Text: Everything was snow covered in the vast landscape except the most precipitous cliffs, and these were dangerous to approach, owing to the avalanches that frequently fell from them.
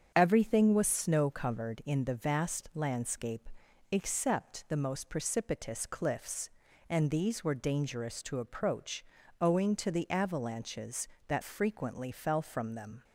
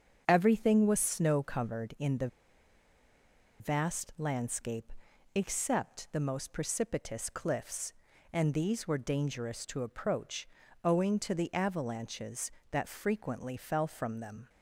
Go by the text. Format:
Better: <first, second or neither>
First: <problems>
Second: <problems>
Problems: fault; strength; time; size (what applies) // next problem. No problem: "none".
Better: first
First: starts louder than the rest; strong; until 1.1 s; 7.5 dB // pauses between "landscape" and "except"; at 3.4 s; 0.44 s long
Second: starts louder than the rest; strong; until 1.2 s; 7.5 dB // pauses between "the" and "vast"; strong; at 2.2 s; 1.3 s long // pauses between "landscape" and "except"; at 4.9 s; 0.44 s long